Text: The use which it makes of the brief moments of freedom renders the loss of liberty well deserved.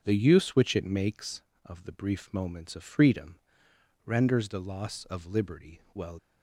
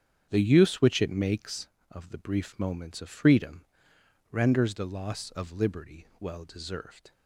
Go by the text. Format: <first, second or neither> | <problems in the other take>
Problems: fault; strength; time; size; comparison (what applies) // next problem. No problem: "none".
second | starts louder than the rest; strong; until 1.0 s; 7.5 dB; strong in the second // pauses between "freedom" and "renders"; noticeable; at 3.3 s; 0.66 s long; noticeable in the second // stops before "deserved"; at 6.1 s